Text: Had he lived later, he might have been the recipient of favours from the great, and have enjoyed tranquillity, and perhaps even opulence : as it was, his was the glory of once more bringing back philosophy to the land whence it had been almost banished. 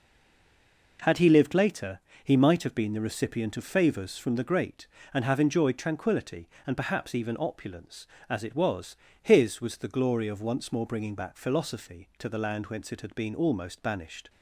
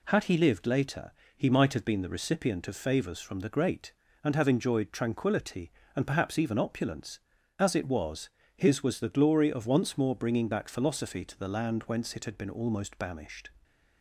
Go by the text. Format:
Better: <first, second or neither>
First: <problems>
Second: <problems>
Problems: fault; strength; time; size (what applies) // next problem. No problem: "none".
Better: second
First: stays silent before the first word; until 0.9 s; 0.9 s long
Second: none